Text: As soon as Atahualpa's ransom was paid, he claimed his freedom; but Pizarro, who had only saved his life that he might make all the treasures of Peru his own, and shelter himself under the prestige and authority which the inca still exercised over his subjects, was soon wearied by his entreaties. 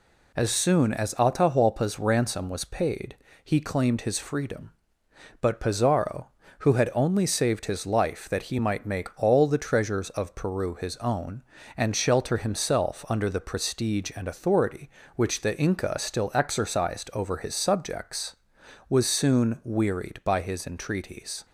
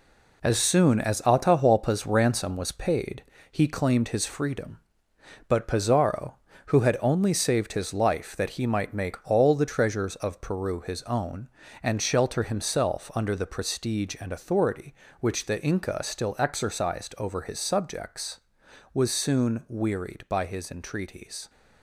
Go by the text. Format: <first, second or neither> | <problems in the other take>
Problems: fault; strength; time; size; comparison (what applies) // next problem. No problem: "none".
first | gets quieter; strong; throughout; 7 dB